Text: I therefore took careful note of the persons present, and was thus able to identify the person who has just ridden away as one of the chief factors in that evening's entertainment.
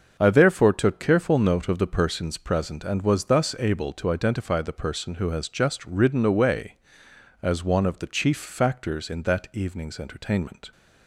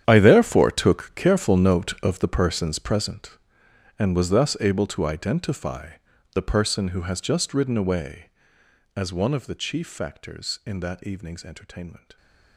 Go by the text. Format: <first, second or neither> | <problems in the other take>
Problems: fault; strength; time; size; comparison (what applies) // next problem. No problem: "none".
first | gets quieter; strong; throughout; 16.5 dB // starts louder than the rest; strong; until 1.0 s; 9.5 dB; also in the first // pauses between "identify" and "the"; at 5.9 s; 0.42 s long